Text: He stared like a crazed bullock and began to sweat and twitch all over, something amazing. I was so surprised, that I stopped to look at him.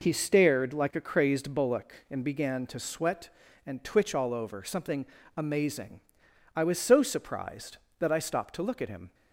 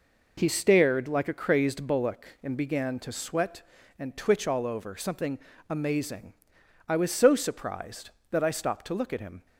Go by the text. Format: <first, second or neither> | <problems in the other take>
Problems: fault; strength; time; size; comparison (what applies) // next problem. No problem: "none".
neither | pauses between "something" and "amazing"; slight; the same in both